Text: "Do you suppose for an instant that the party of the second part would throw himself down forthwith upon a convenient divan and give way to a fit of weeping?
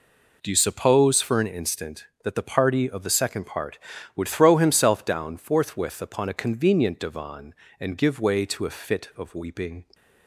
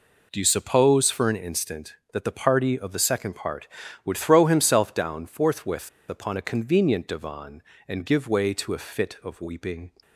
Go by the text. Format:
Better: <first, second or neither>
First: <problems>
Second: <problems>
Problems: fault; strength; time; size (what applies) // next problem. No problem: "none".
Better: first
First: none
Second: pauses between "forthwith" and "upon"; slight; at 5.8 s; 0.19 s long